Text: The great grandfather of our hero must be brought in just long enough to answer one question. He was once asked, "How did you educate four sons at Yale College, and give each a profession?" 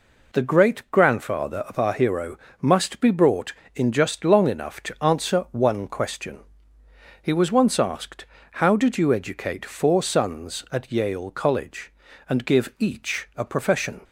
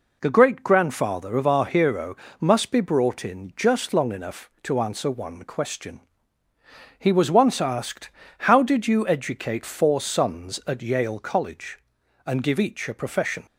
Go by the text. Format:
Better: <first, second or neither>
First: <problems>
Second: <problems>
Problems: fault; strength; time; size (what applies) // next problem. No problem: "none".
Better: neither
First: pauses between "hero" and "must"; slight; at 2.3 s; 0.24 s long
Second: pauses between "hero" and "must"; slight; at 2.1 s; 0.28 s long